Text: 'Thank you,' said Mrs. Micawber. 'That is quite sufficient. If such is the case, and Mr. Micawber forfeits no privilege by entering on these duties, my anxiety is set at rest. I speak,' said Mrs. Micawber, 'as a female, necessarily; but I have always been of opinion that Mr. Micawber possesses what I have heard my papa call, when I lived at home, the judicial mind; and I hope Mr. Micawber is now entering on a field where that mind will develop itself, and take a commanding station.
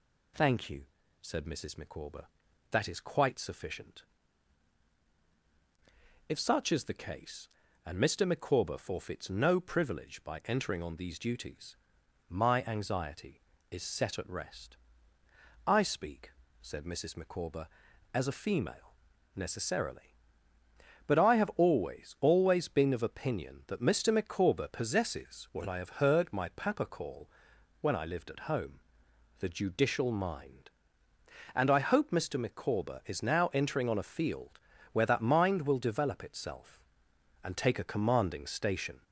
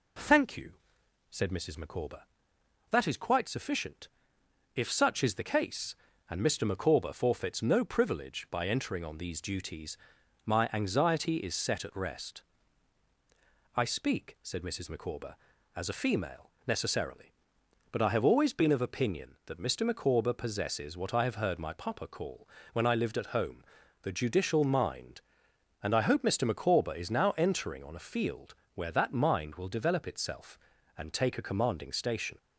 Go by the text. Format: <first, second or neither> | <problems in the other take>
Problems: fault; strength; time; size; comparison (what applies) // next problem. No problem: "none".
second | says "always" twice; at 22.1 s // pauses between "field" and "where"; slight; at 34.5 s; 0.34 s long; slight in the second